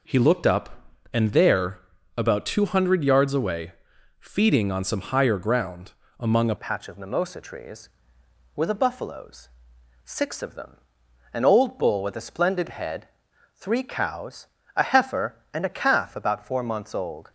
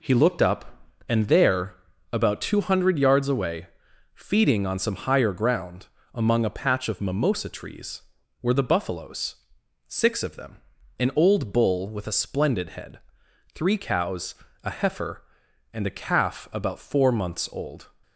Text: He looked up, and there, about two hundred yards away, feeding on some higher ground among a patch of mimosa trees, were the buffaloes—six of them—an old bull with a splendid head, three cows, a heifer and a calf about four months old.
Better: second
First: pauses between "ground" and "among"; slight; at 5.9 s; 0.26 s long // changes voice at "patch"; from 6.5 s on; 10.8 s long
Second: pauses between "ground" and "among"; slight; at 5.8 s; 0.26 s long

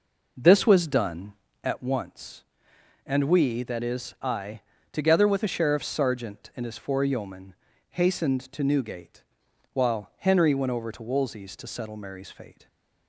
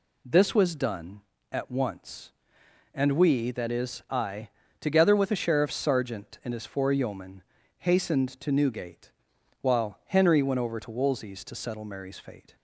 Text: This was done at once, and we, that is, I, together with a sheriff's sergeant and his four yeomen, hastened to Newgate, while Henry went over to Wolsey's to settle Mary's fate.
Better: second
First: starts louder than the rest; noticeable; until 2.0 s; 5 dB // stays silent after the last word; slight; from 12.5 s on; 0.5 s long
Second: none

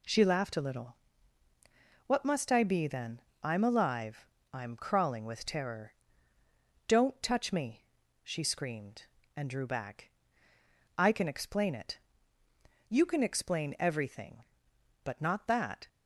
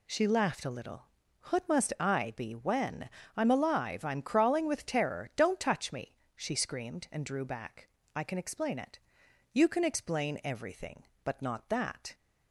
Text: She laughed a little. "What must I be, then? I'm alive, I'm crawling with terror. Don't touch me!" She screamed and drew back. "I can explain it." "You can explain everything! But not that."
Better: first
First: none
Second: says "when" for "then"; at 2.5 s

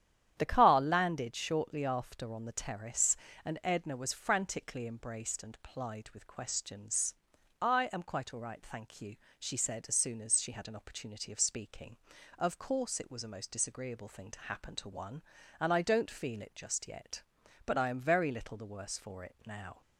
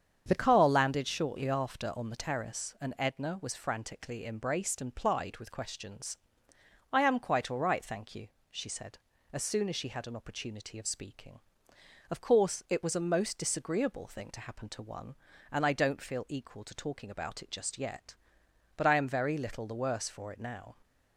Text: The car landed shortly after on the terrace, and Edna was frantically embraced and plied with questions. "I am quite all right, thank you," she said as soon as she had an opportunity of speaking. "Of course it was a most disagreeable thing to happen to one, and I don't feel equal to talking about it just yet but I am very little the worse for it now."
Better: second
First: starts louder than the rest; strong; until 1.3 s; 10 dB // skips "equal to talking about"; at 16.4 s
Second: starts louder than the rest; strong; until 1.2 s; 7.5 dB

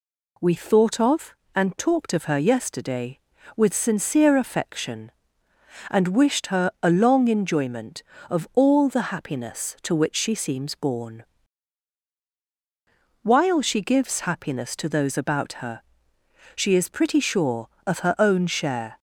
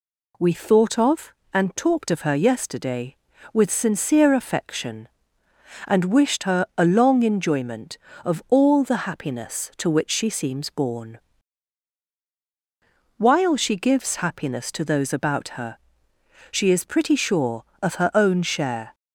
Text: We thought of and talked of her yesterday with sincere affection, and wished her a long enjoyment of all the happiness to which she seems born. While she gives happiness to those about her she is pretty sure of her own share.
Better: neither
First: pauses between "her" and "she"; noticeable; at 15.8 s; 0.72 s long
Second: pauses between "her" and "she"; noticeable; at 15.7 s; 0.72 s long

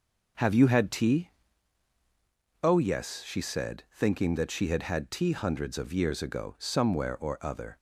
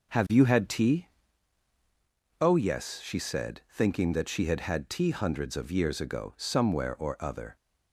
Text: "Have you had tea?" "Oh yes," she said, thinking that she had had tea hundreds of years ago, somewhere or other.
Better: neither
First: starts louder than the rest; until 2.7 s; 6.5 dB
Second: starts louder than the rest; until 2.5 s; 6.5 dB

